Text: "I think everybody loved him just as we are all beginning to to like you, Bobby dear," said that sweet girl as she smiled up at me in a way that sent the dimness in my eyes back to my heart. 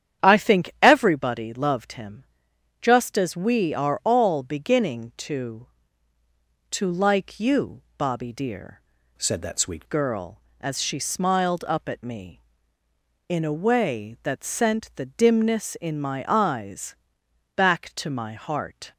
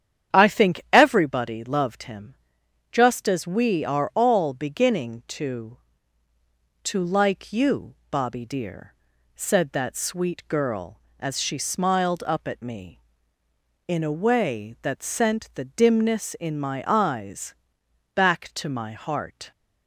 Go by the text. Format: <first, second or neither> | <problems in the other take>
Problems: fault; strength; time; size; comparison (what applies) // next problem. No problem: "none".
second | starts louder than the rest; strong; until 1.3 s; 9.5 dB; strong in the second // pauses between "him" and "just"; noticeable; at 2.2 s; 0.56 s long; noticeable in the second // changes voice from "said" to "sweet"; from 9.1 to 9.8 s; 0.7 s long // pauses between "eyes" and "back"; noticeable; at 16.9 s; 0.62 s long; noticeable in the second